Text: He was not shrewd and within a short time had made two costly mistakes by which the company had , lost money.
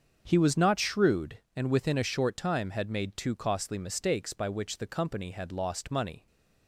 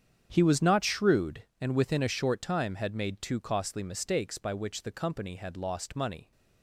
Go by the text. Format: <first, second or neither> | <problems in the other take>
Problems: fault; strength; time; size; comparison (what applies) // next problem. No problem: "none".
first | gets quieter; strong; throughout; 15 dB // starts louder than the rest; strong; until 1.3 s; 8 dB; also in the first